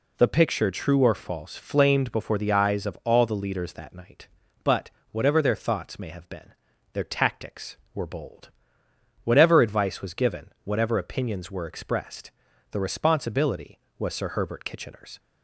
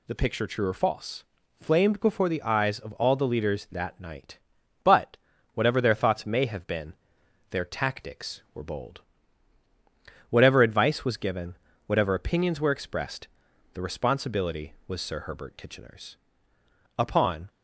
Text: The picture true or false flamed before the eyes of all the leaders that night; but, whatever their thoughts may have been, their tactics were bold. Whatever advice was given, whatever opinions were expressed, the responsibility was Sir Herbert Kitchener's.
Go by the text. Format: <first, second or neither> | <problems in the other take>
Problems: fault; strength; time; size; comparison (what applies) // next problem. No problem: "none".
first | pauses between "false" and "flamed"; slight; at 1.2 s; 0.36 s long // goes on to say "Upon"; from 16.9 s on; 0.52 s long